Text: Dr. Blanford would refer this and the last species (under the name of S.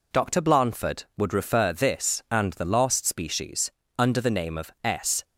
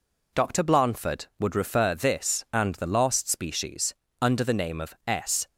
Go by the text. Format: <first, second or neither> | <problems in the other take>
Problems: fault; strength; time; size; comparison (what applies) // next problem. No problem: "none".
neither | none